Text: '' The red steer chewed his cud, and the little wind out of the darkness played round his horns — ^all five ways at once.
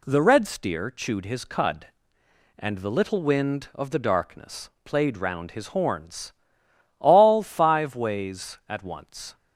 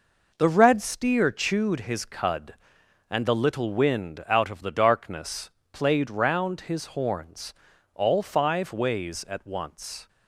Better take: second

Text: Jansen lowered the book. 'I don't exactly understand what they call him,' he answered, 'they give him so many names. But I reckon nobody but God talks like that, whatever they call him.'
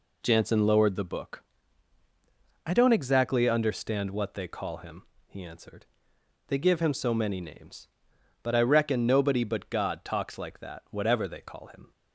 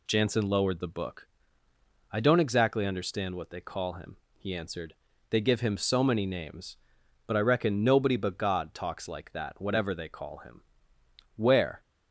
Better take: first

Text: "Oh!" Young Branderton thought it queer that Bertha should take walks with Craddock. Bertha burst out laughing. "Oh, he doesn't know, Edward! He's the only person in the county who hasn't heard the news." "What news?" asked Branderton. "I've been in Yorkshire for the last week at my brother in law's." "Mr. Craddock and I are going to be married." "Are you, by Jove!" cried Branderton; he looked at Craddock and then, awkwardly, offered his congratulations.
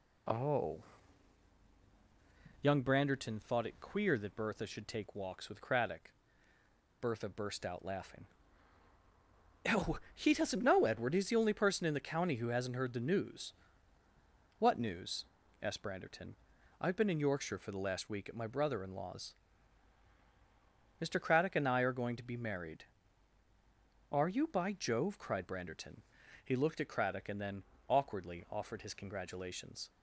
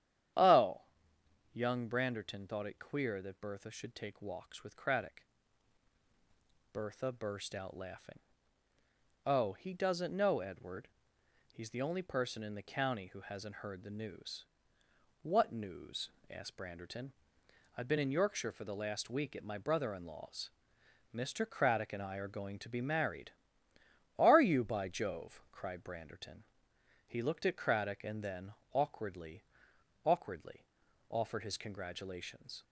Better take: first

